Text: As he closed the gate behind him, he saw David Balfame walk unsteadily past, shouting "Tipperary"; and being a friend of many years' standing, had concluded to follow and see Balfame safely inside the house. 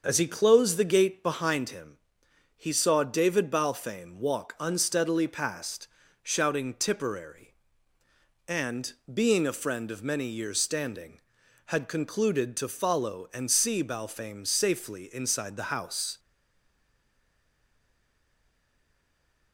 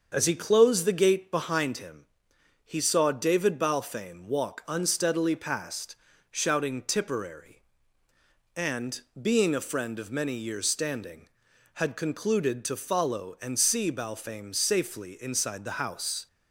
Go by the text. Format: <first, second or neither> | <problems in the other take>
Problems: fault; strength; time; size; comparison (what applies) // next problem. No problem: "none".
second | starts louder than the rest; until 1.0 s; 6.5 dB; also in the second // pauses between "and" and "being"; slight; at 8.9 s; 0.18 s long; slight in the second // stays silent after the last word; strong; from 16.1 s on; 3.4 s long